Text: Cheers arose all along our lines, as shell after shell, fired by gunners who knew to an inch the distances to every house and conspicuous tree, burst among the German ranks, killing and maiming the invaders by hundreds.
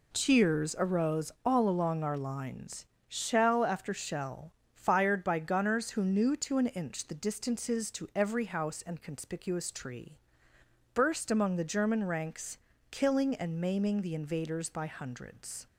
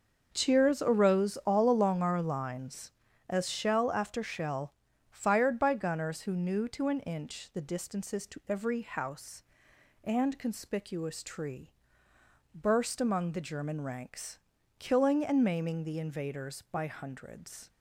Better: second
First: skips "as"; at 2.9 s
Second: none

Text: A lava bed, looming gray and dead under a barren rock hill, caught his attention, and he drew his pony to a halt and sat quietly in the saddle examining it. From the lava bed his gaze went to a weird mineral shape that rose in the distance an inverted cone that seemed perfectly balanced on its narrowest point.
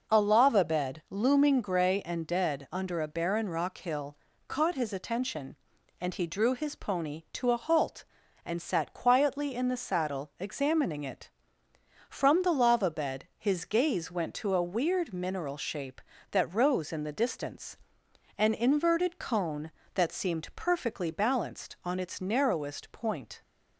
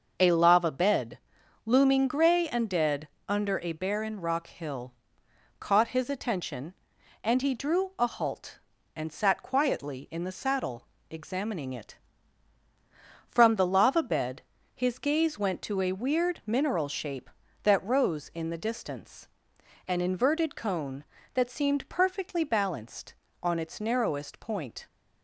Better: first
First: pauses between "distance" and "an"; noticeable; at 17.7 s; 0.62 s long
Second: pauses between "dead" and "under"; slight; at 3.0 s; 0.18 s long // skips "his pony to"; at 7.9 s // pauses between "saddle" and "examining"; slight; at 10.8 s; 0.24 s long // pauses between "bed" and "his"; slight; at 14.4 s; 0.30 s long // pauses between "distance" and "an"; noticeable; at 19.2 s; 0.60 s long

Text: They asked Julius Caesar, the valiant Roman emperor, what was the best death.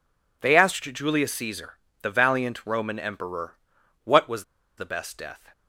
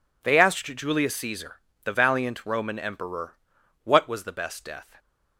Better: second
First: pauses between "was" and "the"; slight; at 4.4 s; 0.33 s long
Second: none

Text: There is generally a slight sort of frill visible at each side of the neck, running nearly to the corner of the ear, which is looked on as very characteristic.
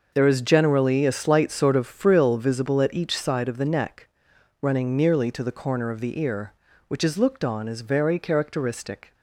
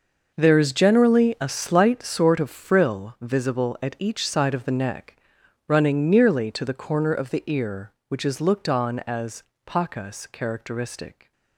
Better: first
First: none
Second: says "pacas" for "very"; at 9.6 s

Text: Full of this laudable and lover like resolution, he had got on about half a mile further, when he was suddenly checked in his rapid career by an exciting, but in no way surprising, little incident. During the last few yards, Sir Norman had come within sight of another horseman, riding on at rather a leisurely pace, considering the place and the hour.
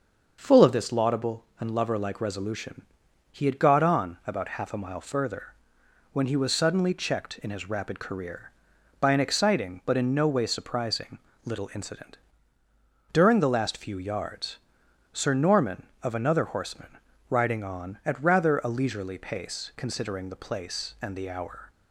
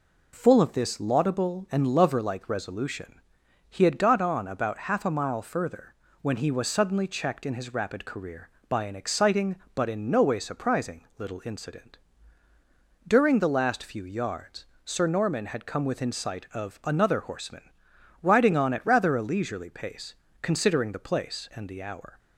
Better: second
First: starts louder than the rest; until 1.4 s; 6.5 dB // skips "had come within sight"; at 15.9 s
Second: none

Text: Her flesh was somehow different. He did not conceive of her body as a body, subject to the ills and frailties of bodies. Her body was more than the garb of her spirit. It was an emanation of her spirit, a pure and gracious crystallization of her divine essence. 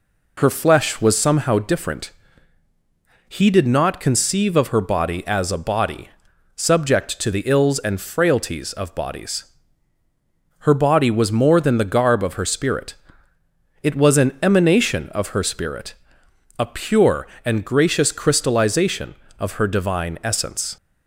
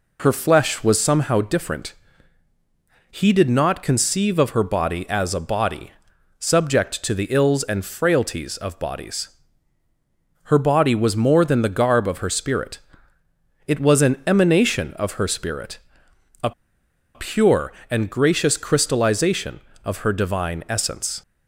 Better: first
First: none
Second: pauses between "a" and "pure"; noticeable; at 16.5 s; 0.64 s long

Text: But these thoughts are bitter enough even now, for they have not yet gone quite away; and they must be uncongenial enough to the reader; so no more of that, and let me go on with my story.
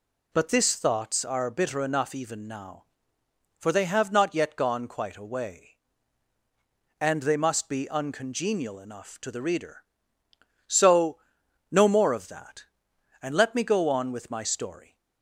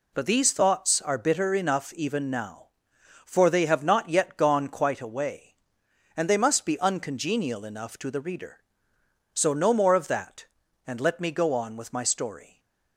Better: second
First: says "this" for "these"; at 0.4 s // pauses between "so" and "no"; noticeable; at 11.1 s; 0.50 s long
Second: none

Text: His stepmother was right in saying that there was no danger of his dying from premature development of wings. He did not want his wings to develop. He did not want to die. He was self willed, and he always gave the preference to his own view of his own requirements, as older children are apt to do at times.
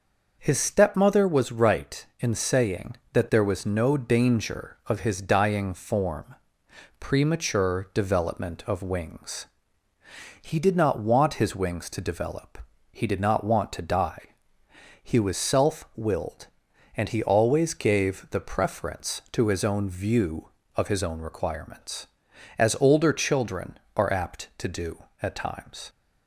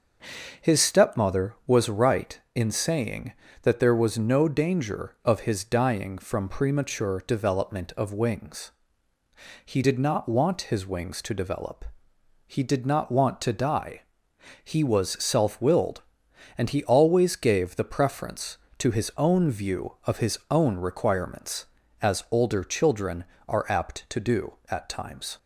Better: second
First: starts louder than the rest; noticeable; until 1.4 s; 6 dB // says "form" for "from"; at 5.7 s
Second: none

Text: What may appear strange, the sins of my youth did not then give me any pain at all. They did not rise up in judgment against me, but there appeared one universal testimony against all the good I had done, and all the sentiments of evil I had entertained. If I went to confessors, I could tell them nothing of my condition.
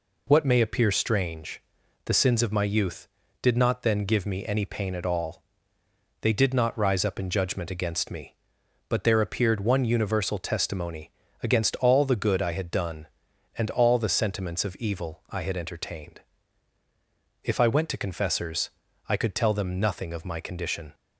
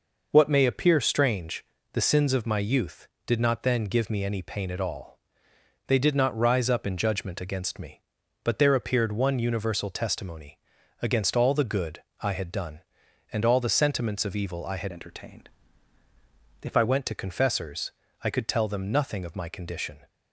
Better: first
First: pauses between "testimony" and "against"; slight; at 11.1 s; 0.30 s long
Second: pauses between "testimony" and "against"; at 10.5 s; 0.42 s long // pauses between "good" and "I"; slight; at 12.0 s; 0.20 s long // changes voice from "entertained" to "I"; from 14.9 to 16.8 s; 1.9 s long

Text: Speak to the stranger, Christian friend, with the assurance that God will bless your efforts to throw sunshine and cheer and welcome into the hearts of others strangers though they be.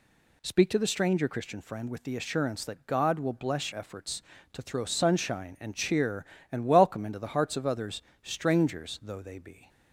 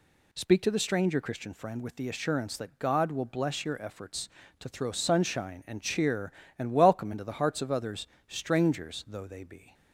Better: second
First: skips "your"; at 3.7 s // pauses between "others" and "strangers"; slight; at 8.0 s; 0.22 s long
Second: pauses between "others" and "strangers"; slight; at 8.0 s; 0.22 s long

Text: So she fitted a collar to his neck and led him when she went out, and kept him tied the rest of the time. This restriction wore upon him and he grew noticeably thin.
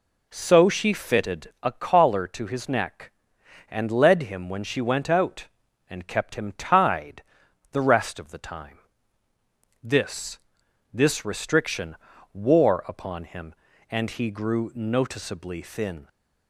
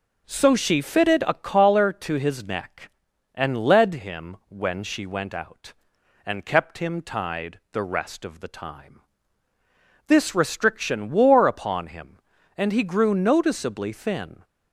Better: second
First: pauses between "tied" and "the"; noticeable; at 7.2 s; 0.50 s long // says "This" twice; at 10.9 s // pauses between "restriction" and "wore"; at 11.9 s; 0.38 s long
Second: none

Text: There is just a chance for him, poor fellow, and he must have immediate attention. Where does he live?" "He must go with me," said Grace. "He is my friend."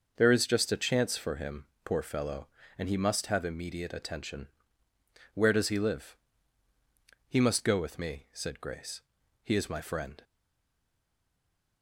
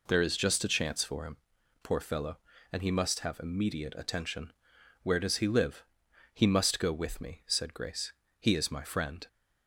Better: second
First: starts louder than the rest; noticeable; until 1.1 s; 6 dB // stays silent after the last word; noticeable; from 10.2 s on; 1.6 s long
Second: none

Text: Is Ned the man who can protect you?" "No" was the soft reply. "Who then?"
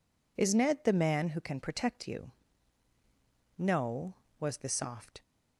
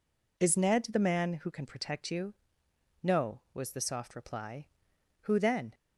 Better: second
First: stops before "reply Who then"; at 5.2 s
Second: none

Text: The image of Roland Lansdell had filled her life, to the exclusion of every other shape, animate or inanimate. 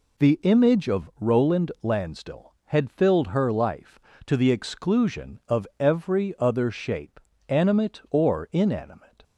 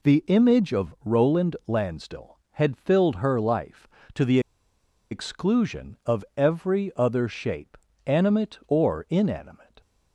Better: first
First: none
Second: pauses between "the" and "exclusion"; noticeable; at 4.3 s; 0.71 s long

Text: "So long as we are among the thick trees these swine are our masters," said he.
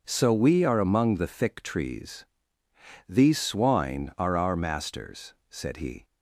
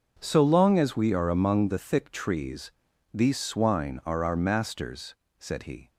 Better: second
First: skips "long as"; at 0.3 s // pauses between "trees" and "these"; noticeable; at 2.2 s; 0.82 s long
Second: pauses between "trees" and "these"; at 2.7 s; 0.42 s long

